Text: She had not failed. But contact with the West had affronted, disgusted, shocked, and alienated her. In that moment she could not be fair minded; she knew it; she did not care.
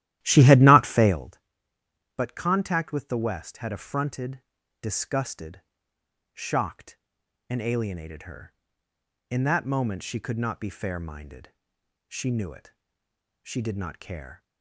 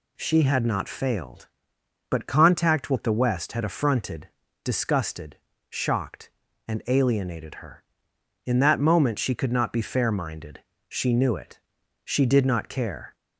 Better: second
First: starts louder than the rest; strong; until 1.3 s; 13.5 dB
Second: none

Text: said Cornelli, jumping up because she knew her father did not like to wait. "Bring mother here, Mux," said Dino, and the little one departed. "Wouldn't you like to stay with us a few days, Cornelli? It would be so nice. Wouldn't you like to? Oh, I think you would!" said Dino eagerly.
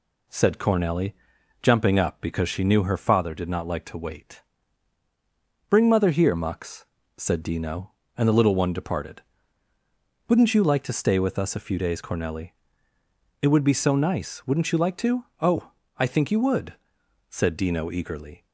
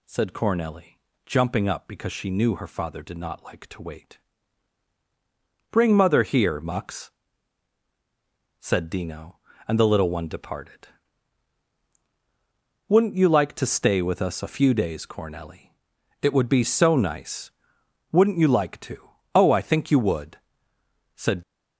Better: first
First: none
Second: stops before "Dino eagerly"; at 21.4 s

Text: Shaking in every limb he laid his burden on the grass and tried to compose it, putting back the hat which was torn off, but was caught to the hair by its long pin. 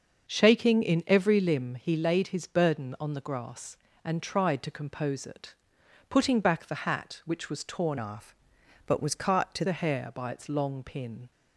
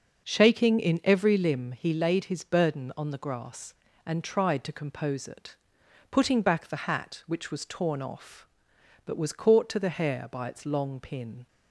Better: second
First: starts louder than the rest; until 1.3 s; 6.5 dB // changes voice from "off" to "to"; from 7.9 to 9.6 s; 1.7 s long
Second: starts louder than the rest; until 1.3 s; 6 dB

